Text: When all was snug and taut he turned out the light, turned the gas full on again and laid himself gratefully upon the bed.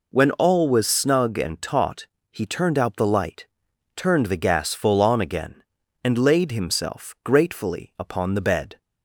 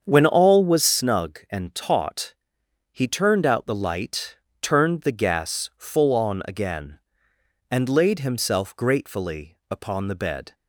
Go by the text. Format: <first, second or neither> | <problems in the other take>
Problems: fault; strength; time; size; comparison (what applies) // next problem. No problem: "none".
first | starts louder than the rest; strong; until 0.9 s; 7 dB // pauses between "taut" and "he"; noticeable; at 2.3 s; 0.60 s long; slight in the first